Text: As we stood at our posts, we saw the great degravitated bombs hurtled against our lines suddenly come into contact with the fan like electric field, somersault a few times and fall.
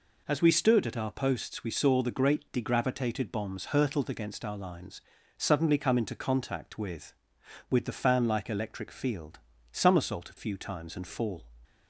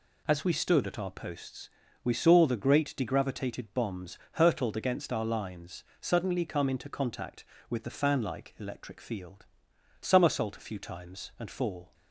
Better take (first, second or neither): second